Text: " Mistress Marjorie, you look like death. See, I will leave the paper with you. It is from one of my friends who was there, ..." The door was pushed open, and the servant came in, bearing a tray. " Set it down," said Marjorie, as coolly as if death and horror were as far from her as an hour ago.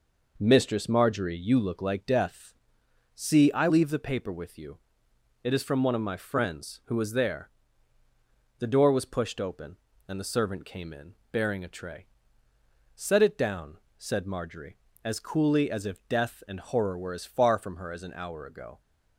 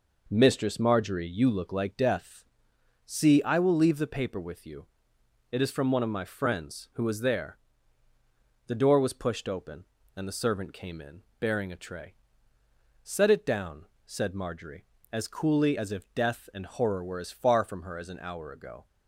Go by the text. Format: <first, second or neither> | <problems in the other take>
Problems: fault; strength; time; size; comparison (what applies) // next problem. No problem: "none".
second | skips "will"; at 3.6 s